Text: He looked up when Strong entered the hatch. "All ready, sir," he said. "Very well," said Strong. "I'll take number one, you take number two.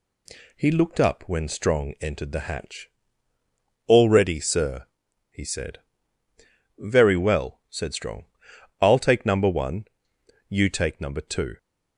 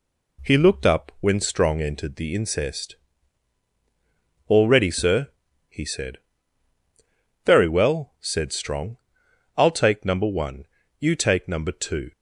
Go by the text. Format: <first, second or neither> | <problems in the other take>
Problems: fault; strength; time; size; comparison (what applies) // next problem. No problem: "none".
first | says "incest" for "hatch"; at 2.3 s